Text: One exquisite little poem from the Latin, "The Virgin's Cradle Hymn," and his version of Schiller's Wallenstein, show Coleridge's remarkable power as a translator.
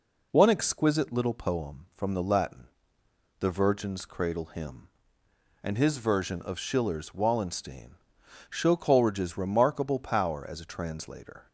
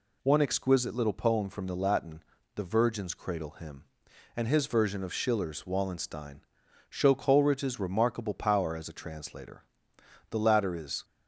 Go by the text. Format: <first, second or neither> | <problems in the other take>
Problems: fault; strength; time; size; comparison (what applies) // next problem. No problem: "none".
first | goes on to say "The latter is"; noticeable; from 10.2 s on; 0.76 s long